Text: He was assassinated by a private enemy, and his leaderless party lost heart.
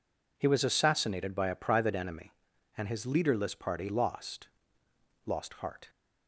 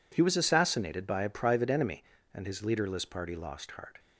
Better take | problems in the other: second | says "lost" twice; at 5.2 s

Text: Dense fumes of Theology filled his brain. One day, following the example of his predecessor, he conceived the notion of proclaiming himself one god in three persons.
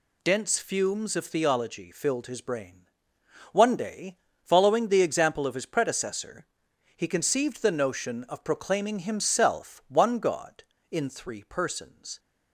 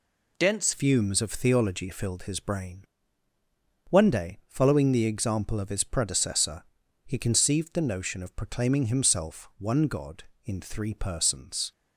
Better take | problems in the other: first | changes voice at "fumes"; from 0.7 s on; 11.0 s long

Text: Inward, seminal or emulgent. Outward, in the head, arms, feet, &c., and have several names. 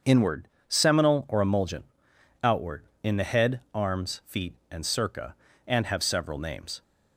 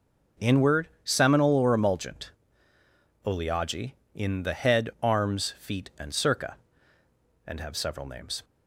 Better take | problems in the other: first | starts louder than the rest; until 1.5 s; 6 dB; also in the first // says "Oleagi" for "Outward"; at 3.2 s

